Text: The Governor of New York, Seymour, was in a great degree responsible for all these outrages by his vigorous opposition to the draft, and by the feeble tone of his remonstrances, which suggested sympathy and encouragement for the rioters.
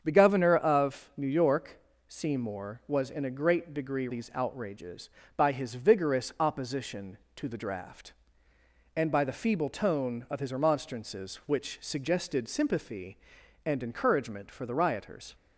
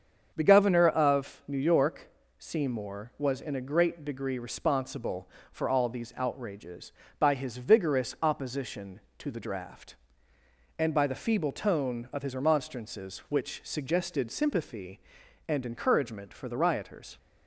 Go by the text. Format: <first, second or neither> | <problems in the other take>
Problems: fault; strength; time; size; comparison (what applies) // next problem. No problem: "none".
second | starts louder than the rest; strong; until 1.0 s; 7.5 dB; also in the second // skips "responsible for all"; at 4.0 s